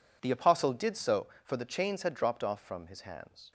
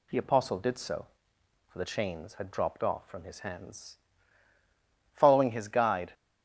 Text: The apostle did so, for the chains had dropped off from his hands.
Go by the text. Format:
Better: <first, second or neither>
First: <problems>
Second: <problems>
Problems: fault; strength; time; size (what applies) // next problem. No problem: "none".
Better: first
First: none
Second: goes on to say "Following his guide"; noticeable; from 5.1 s on; 1.0 s long